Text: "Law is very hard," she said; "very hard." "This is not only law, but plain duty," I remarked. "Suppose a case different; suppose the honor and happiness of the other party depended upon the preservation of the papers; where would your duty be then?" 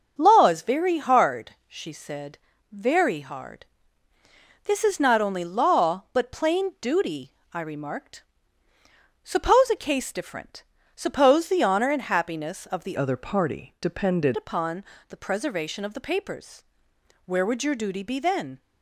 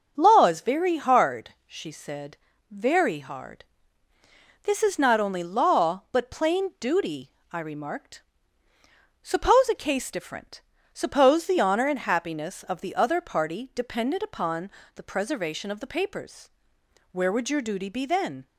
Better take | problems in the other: second | starts louder than the rest; until 1.2 s; 6 dB; also in the second // changes voice from "other" to "depended"; from 12.9 to 14.3 s; 1.4 s long // pauses between "upon" and "the"; slight; at 14.8 s; 0.24 s long; slight in the second

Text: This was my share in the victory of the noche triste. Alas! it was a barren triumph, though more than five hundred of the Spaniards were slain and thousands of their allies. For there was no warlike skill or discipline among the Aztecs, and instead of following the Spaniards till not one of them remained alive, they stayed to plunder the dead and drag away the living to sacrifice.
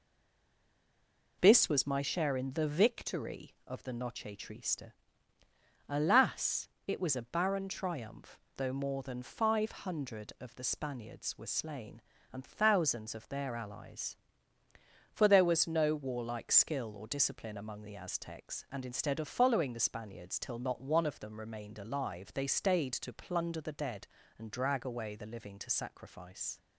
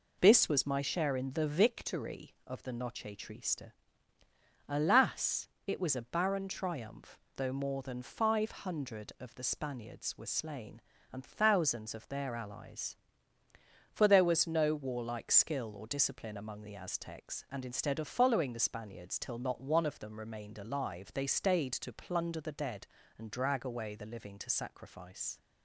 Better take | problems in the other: second | stays silent before the first word; noticeable; until 1.4 s; 1.4 s long

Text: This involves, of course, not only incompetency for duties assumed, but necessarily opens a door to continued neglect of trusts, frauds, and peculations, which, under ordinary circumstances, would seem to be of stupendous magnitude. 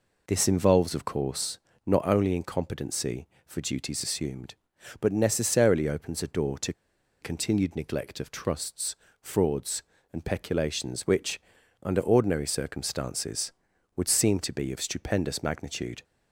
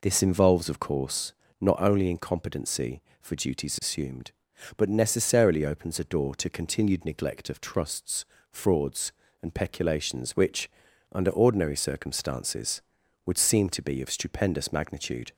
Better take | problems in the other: second | pauses between "to" and "continued"; noticeable; at 6.7 s; 0.49 s long

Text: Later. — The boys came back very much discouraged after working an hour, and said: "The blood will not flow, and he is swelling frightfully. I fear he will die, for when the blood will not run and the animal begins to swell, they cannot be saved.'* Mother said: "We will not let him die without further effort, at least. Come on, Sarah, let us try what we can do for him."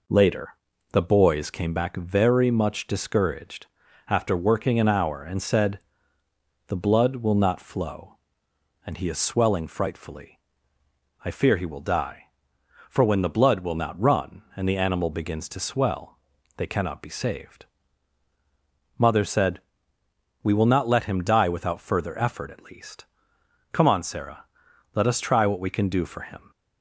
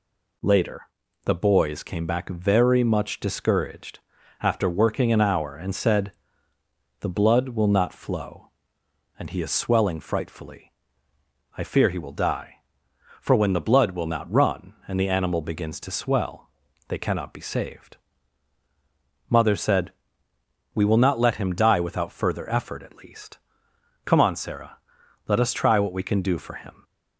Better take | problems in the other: second | starts louder than the rest; noticeable; until 1.9 s; 4.5 dB // pauses between "discouraged" and "after"; at 3.6 s; 0.42 s long; also in the second

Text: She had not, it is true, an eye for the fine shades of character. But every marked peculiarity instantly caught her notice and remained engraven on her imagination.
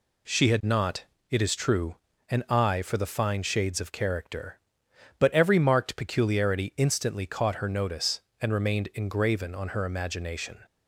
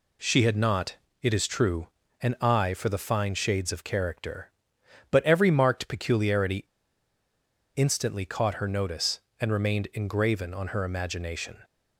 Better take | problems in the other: first | pauses between "peculiarity" and "instantly"; at 6.6 s; 1.0 s long

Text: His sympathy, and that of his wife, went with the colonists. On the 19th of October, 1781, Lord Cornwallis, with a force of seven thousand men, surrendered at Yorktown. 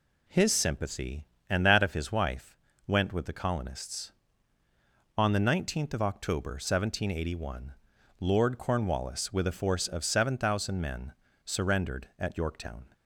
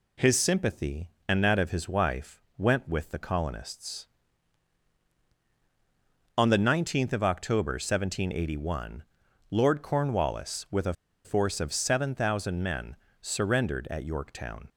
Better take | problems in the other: first | pauses between "a" and "force"; slight; at 10.9 s; 0.32 s long

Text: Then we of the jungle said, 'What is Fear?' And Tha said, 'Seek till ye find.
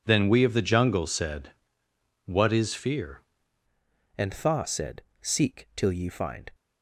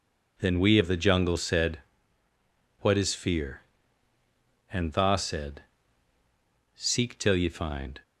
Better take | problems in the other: second | changes voice at "And"; from 4.1 s on; 2.4 s long

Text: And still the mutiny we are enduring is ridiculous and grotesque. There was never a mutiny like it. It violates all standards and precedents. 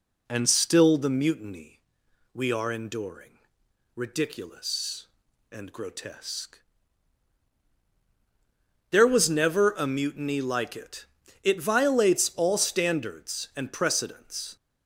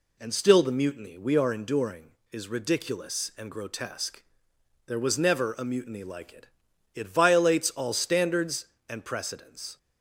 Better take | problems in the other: second | pauses between "mutiny" and "we"; noticeable; at 1.7 s; 0.54 s long // skips "is"; at 3.6 s

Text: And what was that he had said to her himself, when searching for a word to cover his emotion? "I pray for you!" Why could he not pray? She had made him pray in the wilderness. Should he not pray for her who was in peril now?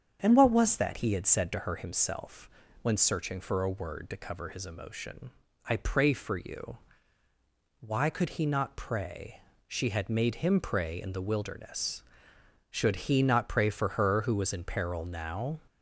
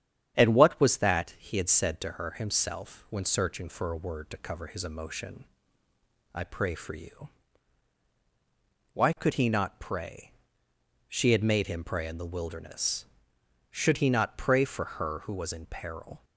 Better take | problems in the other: first | starts louder than the rest; strong; until 1.4 s; 9 dB; strong in the first // stops before "now"; at 16.2 s

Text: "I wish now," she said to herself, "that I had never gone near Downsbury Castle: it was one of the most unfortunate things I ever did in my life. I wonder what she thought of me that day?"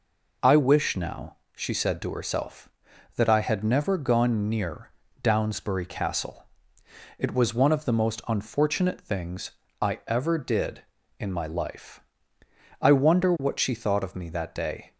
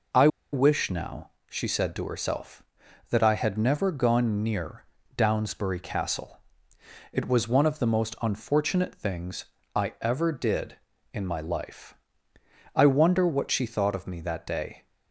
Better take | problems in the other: first | pauses between "I" and "wish"; slight; at 0.2 s; 0.25 s long // pauses between "near" and "Downsbury"; slight; at 4.8 s; 0.32 s long; slight in the first // pauses between "things" and "I"; slight; at 9.4 s; 0.32 s long; slight in the first

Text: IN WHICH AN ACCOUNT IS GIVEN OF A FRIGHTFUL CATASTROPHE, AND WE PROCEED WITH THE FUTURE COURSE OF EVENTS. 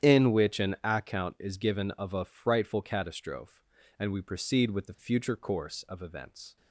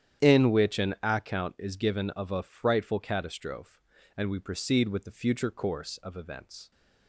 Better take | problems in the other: neither | starts louder than the rest; strong; the same in both

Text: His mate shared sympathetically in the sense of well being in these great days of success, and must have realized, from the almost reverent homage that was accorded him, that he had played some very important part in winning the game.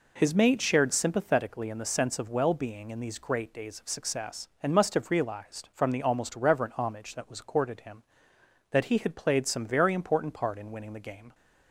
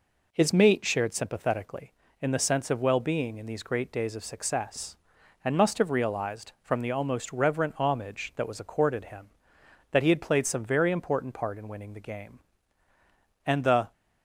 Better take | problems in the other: first | goes on to say "And the"; slight; from 13.4 s on; 0.46 s long

